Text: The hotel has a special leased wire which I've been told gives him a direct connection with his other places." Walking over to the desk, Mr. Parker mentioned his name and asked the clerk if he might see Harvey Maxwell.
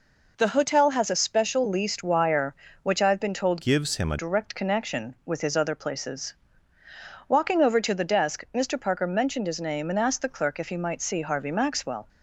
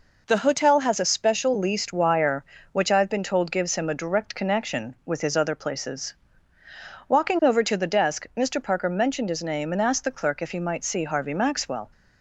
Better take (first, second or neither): second